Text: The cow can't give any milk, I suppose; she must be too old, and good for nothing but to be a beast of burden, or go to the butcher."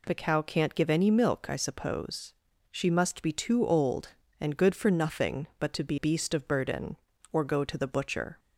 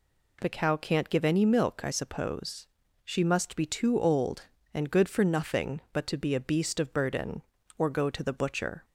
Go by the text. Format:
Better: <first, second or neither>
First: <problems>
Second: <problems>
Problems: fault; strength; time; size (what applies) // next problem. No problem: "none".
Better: second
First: skips "a"; at 5.9 s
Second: none